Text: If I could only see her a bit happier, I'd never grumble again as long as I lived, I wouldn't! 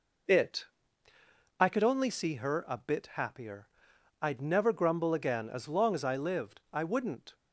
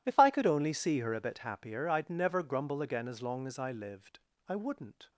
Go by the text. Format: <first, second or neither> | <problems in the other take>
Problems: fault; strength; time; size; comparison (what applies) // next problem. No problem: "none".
second | says "It" for "If"; at 0.2 s